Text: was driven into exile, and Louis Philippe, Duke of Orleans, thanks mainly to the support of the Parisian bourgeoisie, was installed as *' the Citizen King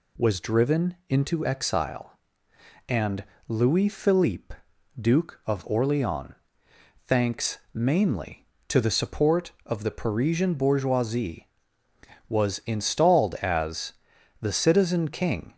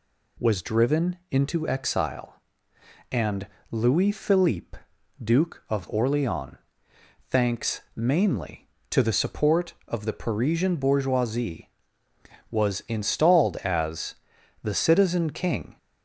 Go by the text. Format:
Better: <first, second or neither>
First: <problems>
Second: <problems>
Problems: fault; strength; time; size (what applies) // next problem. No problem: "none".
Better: neither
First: pauses between "and" and "Louis"; slight; at 3.2 s; 0.24 s long // pauses between "thanks" and "mainly"; slight; at 7.5 s; 0.16 s long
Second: pauses between "and" and "Louis"; slight; at 3.4 s; 0.24 s long // pauses between "thanks" and "mainly"; slight; at 7.8 s; 0.15 s long